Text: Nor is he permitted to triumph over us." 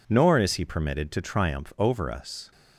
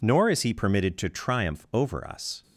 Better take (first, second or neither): neither